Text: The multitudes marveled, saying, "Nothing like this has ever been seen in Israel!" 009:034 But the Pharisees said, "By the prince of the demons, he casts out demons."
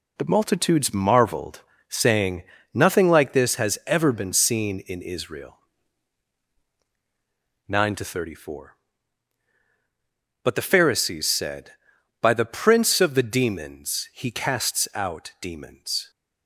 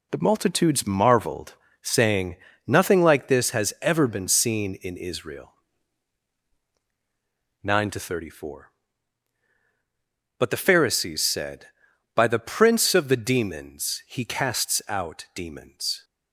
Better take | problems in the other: neither | none

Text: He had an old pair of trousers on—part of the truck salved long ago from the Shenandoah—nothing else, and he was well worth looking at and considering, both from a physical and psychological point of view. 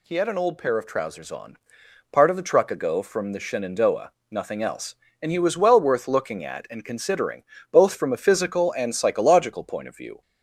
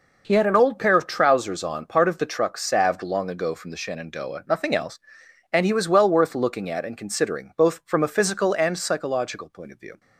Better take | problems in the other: second | skips "salved long"; at 2.6 s

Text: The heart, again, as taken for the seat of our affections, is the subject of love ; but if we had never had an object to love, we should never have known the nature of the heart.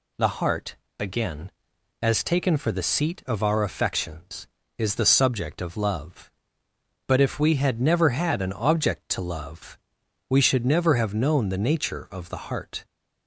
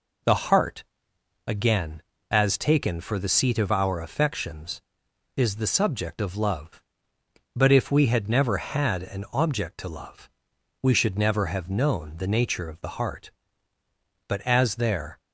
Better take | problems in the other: first | goes on to say "But as there"; noticeable; from 14.2 s on; 0.94 s long

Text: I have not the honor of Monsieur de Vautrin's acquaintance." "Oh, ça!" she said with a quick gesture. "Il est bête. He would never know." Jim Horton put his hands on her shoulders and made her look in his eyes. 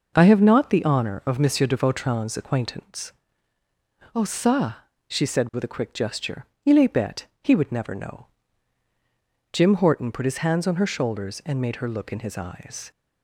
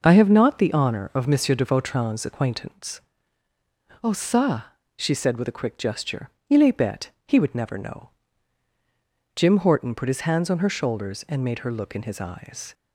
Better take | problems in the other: neither | none

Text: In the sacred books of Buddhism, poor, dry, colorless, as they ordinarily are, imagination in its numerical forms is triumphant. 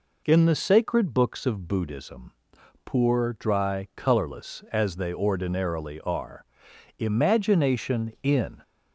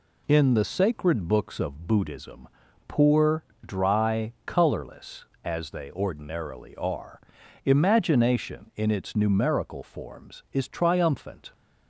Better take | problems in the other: second | stops before "its numerical forms is triumphant"; at 8.6 s

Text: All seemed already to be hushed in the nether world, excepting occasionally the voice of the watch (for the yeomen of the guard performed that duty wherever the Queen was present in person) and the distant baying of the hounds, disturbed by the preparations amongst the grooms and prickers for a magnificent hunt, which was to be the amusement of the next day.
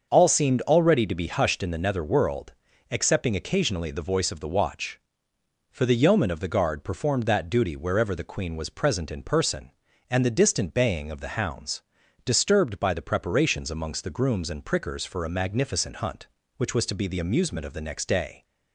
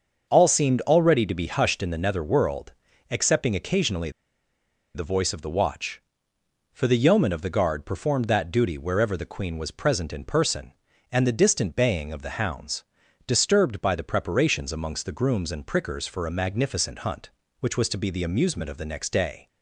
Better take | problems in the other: first | starts louder than the rest; until 1.3 s; 6.5 dB; also in the first // pauses between "occasionally" and "the"; noticeable; at 4.0 s; 0.85 s long

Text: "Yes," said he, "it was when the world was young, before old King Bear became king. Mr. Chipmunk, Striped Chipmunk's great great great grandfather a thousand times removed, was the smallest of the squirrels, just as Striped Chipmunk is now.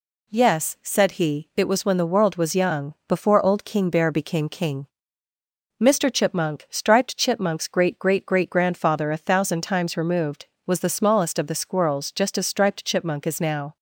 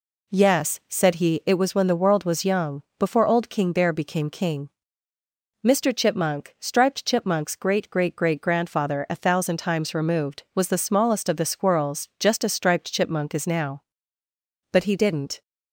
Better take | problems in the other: first | goes on to say "But he didn't"; noticeable; from 14.7 s on; 0.70 s long

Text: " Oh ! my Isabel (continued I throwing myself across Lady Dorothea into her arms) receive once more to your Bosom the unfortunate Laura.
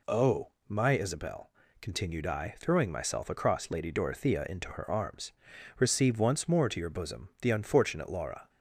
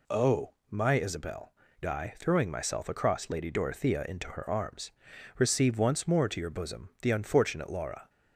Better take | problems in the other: first | skips "continued"; at 1.6 s

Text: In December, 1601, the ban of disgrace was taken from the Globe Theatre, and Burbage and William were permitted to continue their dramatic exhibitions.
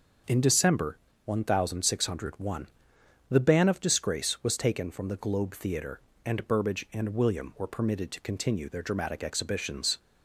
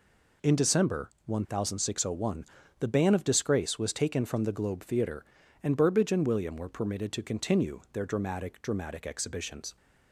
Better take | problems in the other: first | says "dramatic" twice; at 8.5 s

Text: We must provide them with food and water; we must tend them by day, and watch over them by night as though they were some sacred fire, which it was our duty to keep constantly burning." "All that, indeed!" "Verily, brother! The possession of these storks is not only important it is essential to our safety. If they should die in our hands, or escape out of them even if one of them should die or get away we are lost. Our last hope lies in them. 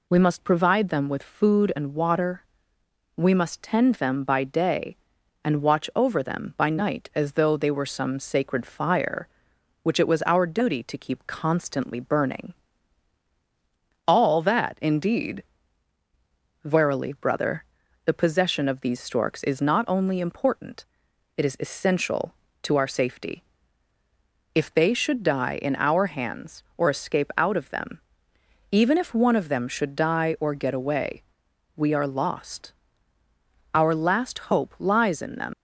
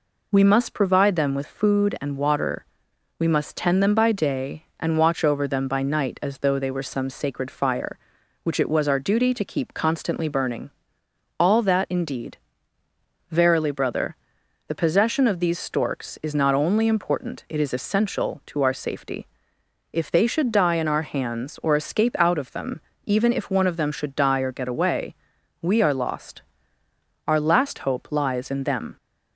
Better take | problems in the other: second | pauses between "important" and "it"; noticeable; at 20.8 s; 0.50 s long // pauses between "them" and "even"; noticeable; at 27.9 s; 0.70 s long; slight in the second // pauses between "away" and "we"; noticeable; at 31.2 s; 0.54 s long; noticeable in the second // leaves "them" unfinished; at 35.5 s; 135 ms

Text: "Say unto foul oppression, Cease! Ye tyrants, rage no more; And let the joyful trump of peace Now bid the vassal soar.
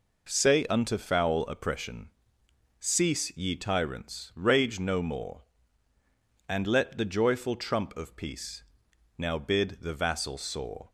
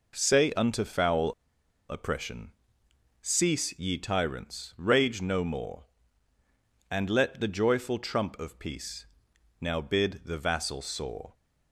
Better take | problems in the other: first | pauses between "foul" and "oppression"; noticeable; at 1.3 s; 0.55 s long // pauses between "peace" and "Now"; noticeable; at 9.0 s; 0.52 s long; noticeable in the first

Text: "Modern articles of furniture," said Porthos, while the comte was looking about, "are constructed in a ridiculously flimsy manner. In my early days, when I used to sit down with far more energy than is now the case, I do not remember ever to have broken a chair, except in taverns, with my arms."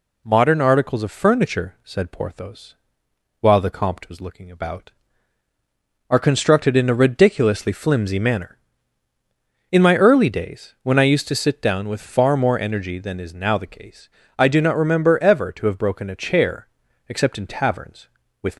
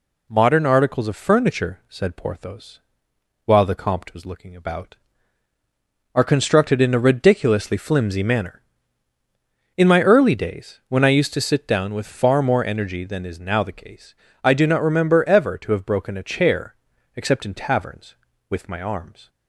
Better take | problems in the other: second | stops before "my arms"; at 18.5 s

